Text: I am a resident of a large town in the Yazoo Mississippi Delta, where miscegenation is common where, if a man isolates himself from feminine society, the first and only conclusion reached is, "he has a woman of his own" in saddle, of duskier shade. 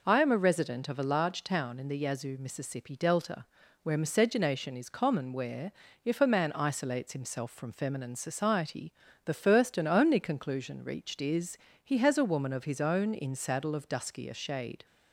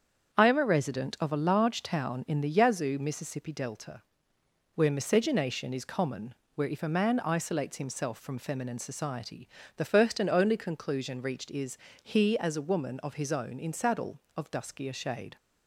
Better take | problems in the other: first | starts louder than the rest; strong; until 1.4 s; 7.5 dB // pauses between "common" and "where"; slight; at 6.3 s; 0.20 s long // says "as" for "has"; at 12.3 s

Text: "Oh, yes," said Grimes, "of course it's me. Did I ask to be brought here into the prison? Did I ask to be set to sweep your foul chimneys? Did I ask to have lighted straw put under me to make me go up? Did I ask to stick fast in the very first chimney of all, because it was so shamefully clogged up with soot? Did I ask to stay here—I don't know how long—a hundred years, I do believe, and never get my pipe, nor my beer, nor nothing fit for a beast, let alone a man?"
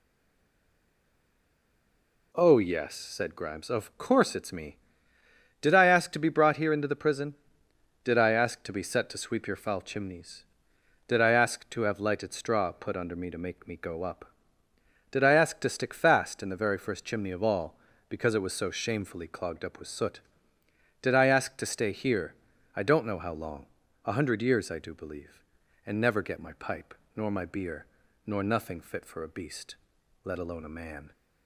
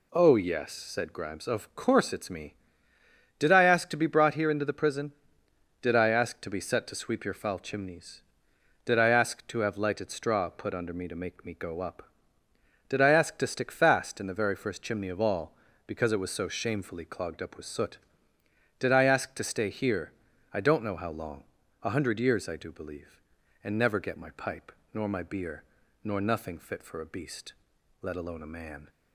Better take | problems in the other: second | stays silent before the first word; until 2.3 s; 2.3 s long

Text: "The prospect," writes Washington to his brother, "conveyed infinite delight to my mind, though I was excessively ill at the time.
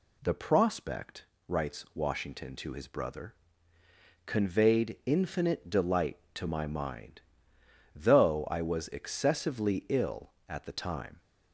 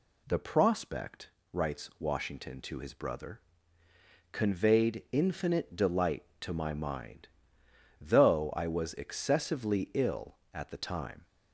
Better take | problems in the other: neither | none

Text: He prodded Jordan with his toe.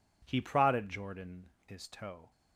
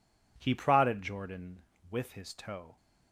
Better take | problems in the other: second | skips "with"; at 1.5 s

